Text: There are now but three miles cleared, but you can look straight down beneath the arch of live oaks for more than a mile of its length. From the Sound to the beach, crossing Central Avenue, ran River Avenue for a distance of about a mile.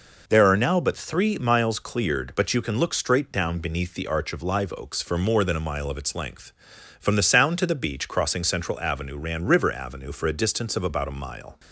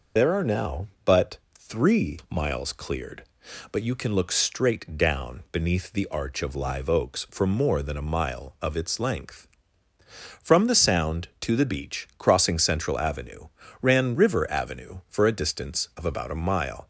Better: first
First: none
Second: loses the start of "There"; at 0.1 s; 65 ms // pauses between "but" and "three"; slight; at 1.3 s; 0.16 s long

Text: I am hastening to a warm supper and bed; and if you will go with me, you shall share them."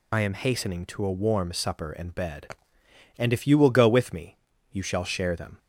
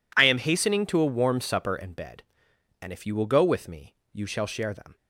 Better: second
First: loses the start of "I"; at 0.1 s; 35 ms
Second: none

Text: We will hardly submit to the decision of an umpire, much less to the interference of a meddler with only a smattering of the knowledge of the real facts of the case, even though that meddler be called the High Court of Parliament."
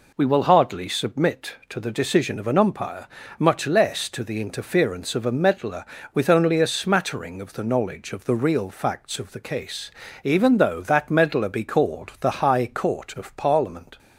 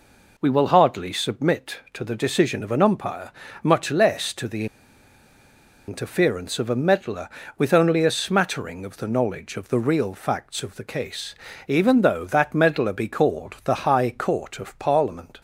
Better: first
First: none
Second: pauses between "the" and "interference"; at 4.6 s; 1.2 s long

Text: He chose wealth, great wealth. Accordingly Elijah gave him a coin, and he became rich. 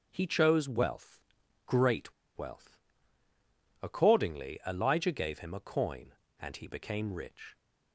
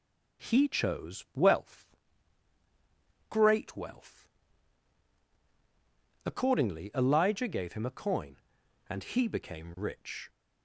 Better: second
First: starts louder than the rest; strong; until 1.1 s; 7 dB // pauses between "great" and "wealth"; slight; at 2.1 s; 0.24 s long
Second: none

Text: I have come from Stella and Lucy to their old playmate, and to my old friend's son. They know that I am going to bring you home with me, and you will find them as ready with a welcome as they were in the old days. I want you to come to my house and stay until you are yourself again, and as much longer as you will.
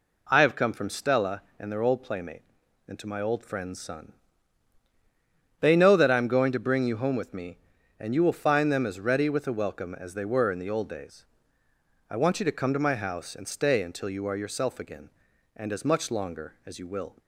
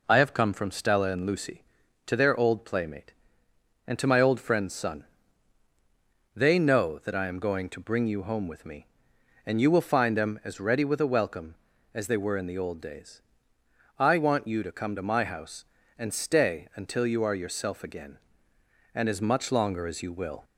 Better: second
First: skips "Lucy to"; at 1.7 s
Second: none

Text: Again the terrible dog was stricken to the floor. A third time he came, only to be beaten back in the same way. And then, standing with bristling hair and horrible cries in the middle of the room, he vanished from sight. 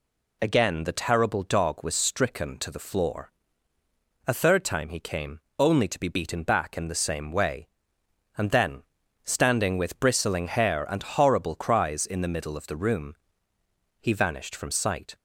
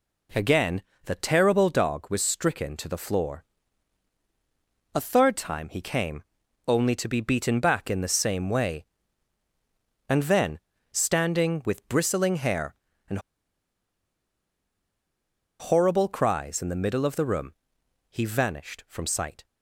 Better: first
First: none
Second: pauses between "Again" and "the"; slight; at 0.8 s; 0.24 s long // pauses between "and" and "horrible"; strong; at 13.1 s; 2.4 s long

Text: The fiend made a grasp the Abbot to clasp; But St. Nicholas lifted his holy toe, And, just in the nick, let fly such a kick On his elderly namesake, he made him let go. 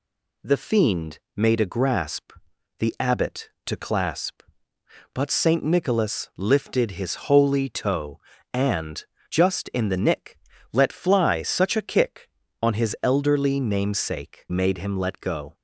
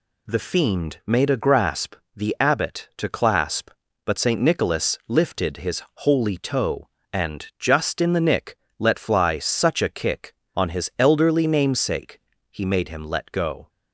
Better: second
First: pauses between "fiend" and "made"; slight; at 1.1 s; 0.16 s long // pauses between "grasp" and "the"; noticeable; at 2.3 s; 0.48 s long // skips "he"; at 14.4 s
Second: pauses between "grasp" and "the"; slight; at 1.9 s; 0.22 s long

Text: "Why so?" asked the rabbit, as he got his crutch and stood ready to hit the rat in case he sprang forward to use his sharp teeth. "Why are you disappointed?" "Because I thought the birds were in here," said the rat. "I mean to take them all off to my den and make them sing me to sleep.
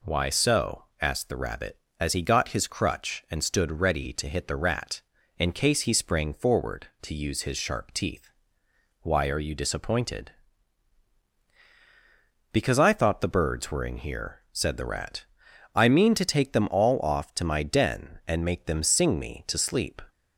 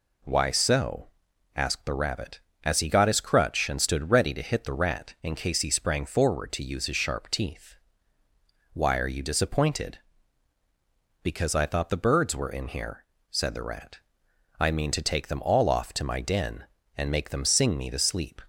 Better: neither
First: none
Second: none

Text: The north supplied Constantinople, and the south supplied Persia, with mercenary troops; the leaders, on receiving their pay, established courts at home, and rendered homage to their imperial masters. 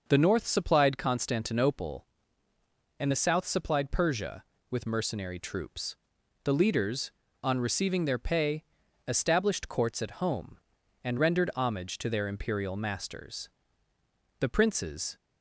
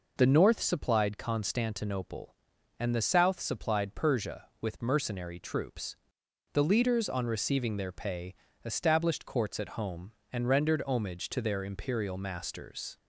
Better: second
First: goes on to say "The princes"; noticeable; from 14.4 s on; 0.78 s long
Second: none

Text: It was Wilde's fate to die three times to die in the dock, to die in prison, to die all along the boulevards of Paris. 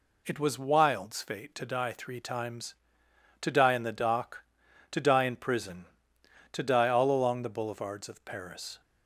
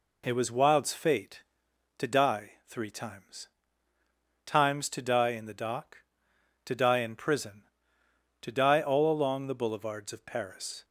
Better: first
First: none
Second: says "times" twice; at 4.4 s

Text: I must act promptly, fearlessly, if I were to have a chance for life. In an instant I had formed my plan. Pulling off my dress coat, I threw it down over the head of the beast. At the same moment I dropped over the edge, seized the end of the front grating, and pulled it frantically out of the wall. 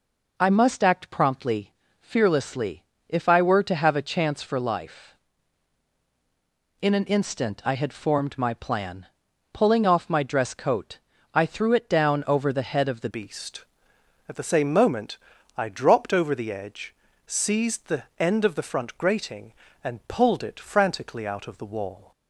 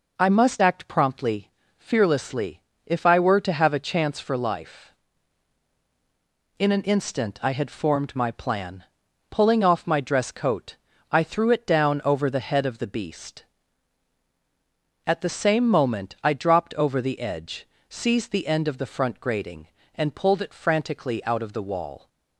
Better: second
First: changes voice at "beast"; from 13.0 s on; 9.1 s long // pauses between "moment" and "I"; at 15.1 s; 0.40 s long // pauses between "the" and "end"; slight; at 18.0 s; 0.16 s long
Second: none

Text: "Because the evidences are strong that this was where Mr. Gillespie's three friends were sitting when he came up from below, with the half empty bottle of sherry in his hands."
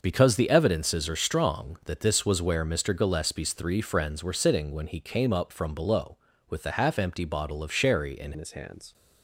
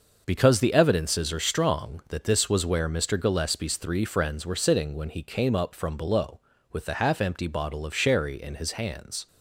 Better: second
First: changes voice at "his"; from 8.3 s on; 0.6 s long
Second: none

